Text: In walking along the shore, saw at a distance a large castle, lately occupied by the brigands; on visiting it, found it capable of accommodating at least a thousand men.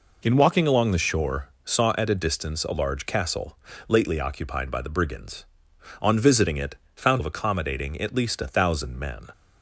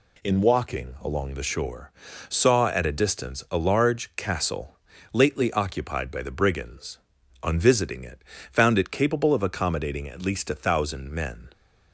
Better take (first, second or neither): second